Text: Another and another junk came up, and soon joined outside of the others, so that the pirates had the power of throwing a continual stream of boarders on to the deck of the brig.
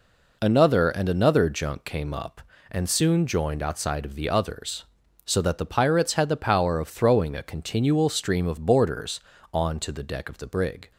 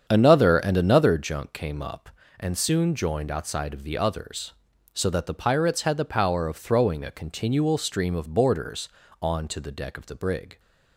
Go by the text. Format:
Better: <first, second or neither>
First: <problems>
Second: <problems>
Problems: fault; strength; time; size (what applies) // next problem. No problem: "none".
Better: first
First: none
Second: starts louder than the rest; strong; until 1.3 s; 8 dB